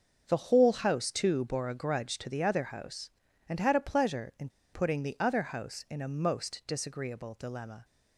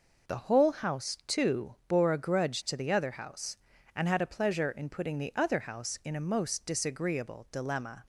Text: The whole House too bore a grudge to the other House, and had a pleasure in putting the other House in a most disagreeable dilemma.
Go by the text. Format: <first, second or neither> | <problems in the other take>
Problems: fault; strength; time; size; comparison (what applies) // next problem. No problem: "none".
second | pauses between "in" and "putting"; slight; at 4.4 s; 0.25 s long